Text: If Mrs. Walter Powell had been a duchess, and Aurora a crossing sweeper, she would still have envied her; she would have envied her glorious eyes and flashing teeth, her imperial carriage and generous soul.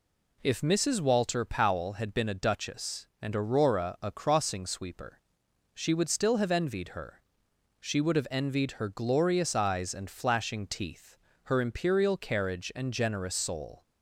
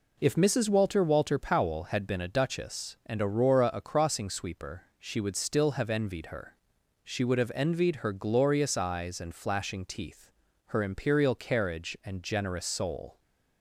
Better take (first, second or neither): first